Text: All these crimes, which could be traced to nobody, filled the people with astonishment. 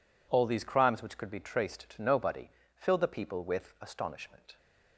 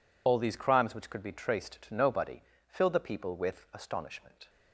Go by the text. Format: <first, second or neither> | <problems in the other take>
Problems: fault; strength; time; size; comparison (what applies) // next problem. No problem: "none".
first | loses the start of "All"; at 0.2 s; 45 ms